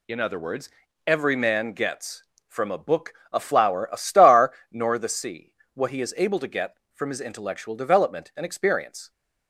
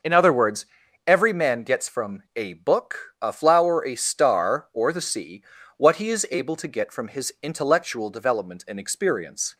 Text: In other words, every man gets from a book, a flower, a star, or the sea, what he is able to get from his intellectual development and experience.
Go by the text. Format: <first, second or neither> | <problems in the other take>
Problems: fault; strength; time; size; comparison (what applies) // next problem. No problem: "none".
second | says "nor" for "or"; at 4.7 s